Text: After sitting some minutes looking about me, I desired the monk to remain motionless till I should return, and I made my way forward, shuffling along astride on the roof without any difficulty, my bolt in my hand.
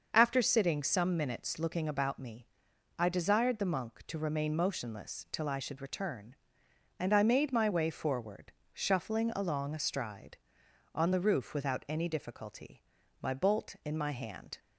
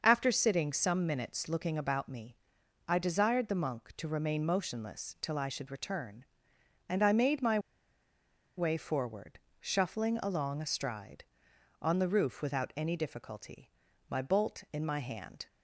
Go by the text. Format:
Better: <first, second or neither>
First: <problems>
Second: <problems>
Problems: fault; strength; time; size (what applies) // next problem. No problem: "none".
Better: first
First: starts louder than the rest; until 1.1 s; 6 dB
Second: starts louder than the rest; until 1.0 s; 6 dB // pauses between "my" and "way"; at 7.5 s; 0.98 s long